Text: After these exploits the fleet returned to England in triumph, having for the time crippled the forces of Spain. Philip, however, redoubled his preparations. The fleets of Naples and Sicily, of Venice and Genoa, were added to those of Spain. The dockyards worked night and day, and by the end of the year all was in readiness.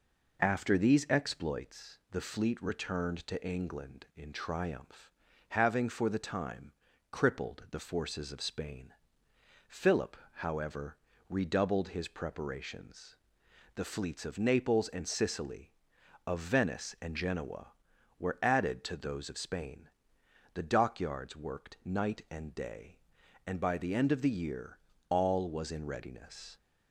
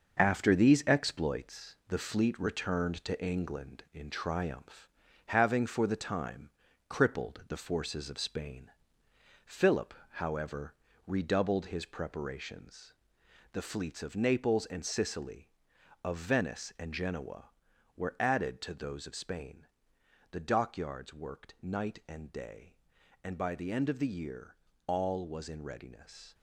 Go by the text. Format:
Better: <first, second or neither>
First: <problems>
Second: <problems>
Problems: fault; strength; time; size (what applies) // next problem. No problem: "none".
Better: first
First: pauses between "time" and "crippled"; at 6.7 s; 0.38 s long // pauses between "year" and "all"; slight; at 24.7 s; 0.32 s long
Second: gets quieter; throughout; 7 dB // pauses between "time" and "crippled"; at 6.4 s; 0.38 s long // pauses between "year" and "all"; slight; at 24.5 s; 0.32 s long